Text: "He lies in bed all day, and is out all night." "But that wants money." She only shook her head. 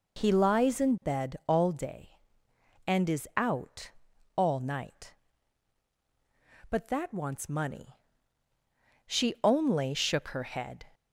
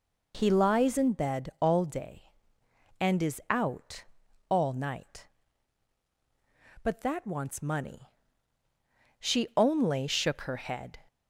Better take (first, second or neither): neither